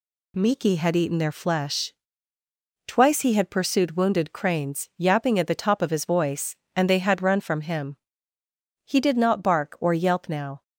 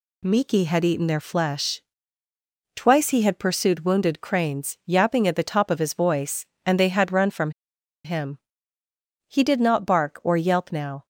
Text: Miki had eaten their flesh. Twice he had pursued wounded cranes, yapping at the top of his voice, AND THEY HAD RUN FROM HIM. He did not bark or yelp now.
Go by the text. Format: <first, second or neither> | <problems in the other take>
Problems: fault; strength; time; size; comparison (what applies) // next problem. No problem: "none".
first | pauses between "FROM" and "HIM"; noticeable; at 7.4 s; 0.54 s long